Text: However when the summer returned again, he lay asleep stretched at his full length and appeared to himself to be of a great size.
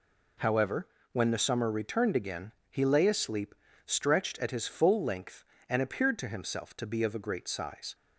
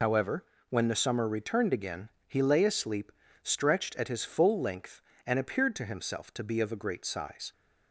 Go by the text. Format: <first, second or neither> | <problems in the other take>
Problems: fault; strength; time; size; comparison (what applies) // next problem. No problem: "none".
first | loses the start of "However"; at 0.0 s; 50 ms // pauses between "However" and "when"; slight; at 0.4 s; 0.24 s long; slight in the first // pauses between "asleep" and "stretched"; slight; at 3.1 s; 0.32 s long; slight in the first